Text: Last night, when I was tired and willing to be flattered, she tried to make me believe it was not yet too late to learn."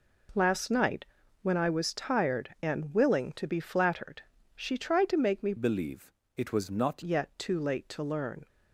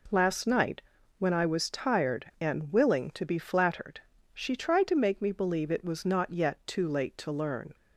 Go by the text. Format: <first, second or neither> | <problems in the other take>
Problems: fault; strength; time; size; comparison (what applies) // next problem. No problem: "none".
second | changes voice from "believe" to "not"; from 5.5 to 7.0 s; 1.5 s long // pauses between "believe" and "it"; slight; at 6.1 s; 0.24 s long